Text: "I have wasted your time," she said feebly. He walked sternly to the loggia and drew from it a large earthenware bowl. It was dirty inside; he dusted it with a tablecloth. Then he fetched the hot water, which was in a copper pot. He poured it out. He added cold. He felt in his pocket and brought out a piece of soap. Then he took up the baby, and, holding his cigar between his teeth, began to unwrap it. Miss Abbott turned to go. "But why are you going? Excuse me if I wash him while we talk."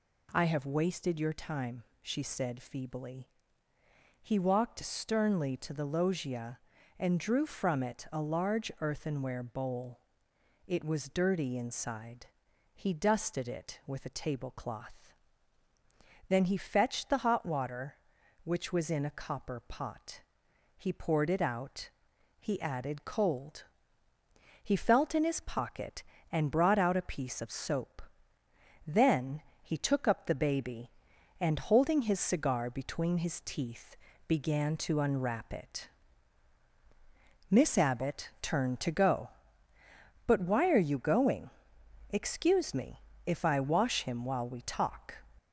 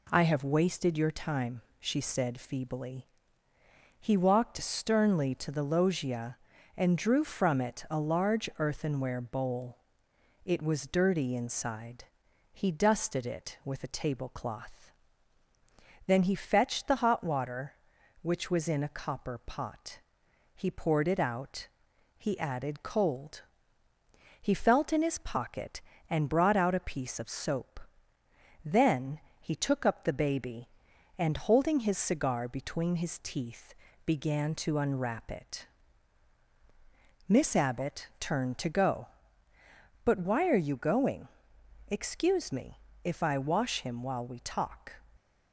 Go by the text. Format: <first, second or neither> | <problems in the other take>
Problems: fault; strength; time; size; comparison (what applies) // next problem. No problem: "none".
second | gets louder; slight; throughout; 3.5 dB // pauses between "Then" and "he"; slight; at 29.4 s; 0.20 s long; slight in the second // pauses between "me" and "if"; slight; at 43.0 s; 0.24 s long; slight in the second